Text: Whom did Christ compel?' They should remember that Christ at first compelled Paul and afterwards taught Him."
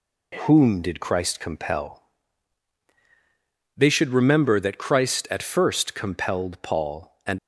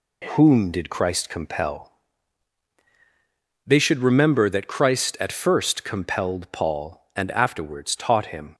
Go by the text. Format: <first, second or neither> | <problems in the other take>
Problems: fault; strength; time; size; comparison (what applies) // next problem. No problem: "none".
second | stops before "afterwards taught Him"; at 7.3 s